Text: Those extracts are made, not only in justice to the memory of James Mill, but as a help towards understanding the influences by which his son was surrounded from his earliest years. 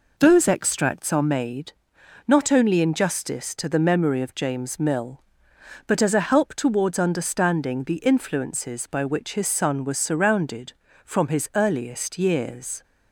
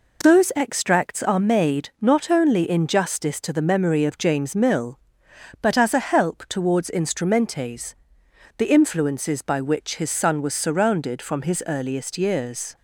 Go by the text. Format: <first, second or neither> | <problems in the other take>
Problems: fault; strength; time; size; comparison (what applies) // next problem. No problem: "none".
first | says "instrumentes" for "understanding"; at 6.8 s